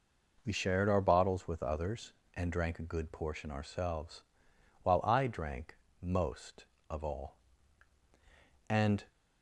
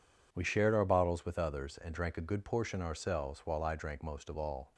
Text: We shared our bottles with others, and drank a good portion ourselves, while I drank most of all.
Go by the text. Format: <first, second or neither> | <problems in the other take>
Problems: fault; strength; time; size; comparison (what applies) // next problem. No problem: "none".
second | goes on to say "And"; slight; from 8.6 s on; 0.38 s long